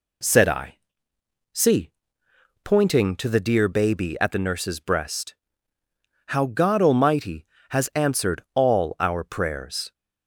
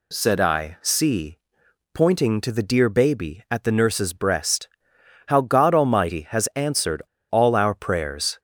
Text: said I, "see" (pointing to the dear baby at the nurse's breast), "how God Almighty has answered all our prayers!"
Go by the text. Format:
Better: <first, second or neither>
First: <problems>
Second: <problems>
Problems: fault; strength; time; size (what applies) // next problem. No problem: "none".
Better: first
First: none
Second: pauses between "answered" and "all"; slight; at 7.0 s; 0.27 s long